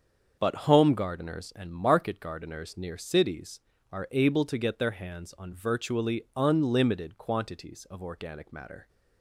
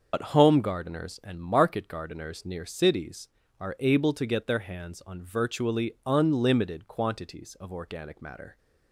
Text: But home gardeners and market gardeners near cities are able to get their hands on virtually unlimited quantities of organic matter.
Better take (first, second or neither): first